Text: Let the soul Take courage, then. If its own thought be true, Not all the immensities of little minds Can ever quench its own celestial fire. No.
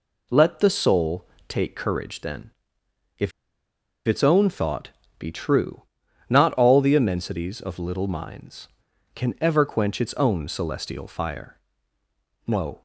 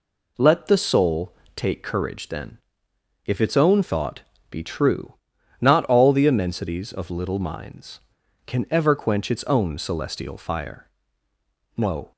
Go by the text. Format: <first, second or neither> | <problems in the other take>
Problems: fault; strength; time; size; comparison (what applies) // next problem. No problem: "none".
second | pauses between "soul" and "Take"; slight; at 1.2 s; 0.22 s long; slight in the second // pauses between "If" and "its"; noticeable; at 3.3 s; 0.74 s long // pauses between "thought" and "be"; slight; at 4.8 s; 0.28 s long; slight in the second